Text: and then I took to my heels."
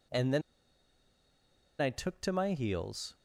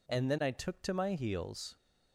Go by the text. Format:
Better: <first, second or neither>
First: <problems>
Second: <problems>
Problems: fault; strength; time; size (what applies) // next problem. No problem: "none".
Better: second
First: pauses between "then" and "I"; strong; at 0.4 s; 1.3 s long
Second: none